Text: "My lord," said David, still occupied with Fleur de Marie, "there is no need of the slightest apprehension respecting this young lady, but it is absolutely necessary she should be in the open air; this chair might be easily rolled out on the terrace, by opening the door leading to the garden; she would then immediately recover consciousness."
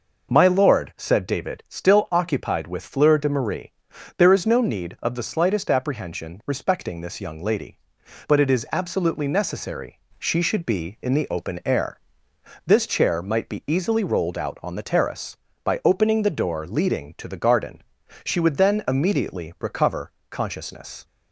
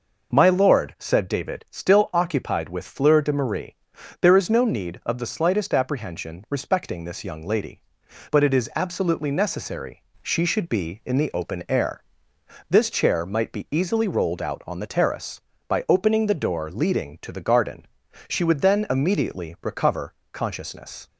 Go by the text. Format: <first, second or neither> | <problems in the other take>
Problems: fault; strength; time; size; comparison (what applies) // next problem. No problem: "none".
neither | pauses between "necessary" and "she"; slight; the same in both // pauses between "recover" and "consciousness"; slight; the same in both